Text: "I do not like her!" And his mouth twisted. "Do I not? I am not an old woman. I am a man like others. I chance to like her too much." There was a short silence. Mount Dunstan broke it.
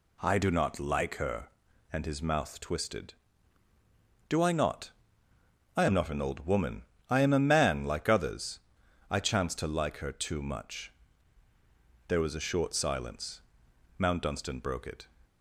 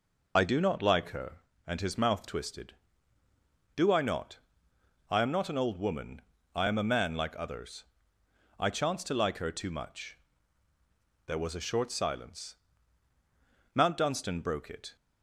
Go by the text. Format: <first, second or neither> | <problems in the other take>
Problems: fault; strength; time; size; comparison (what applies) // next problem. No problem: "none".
first | loses the start of "I"; at 0.3 s; 40 ms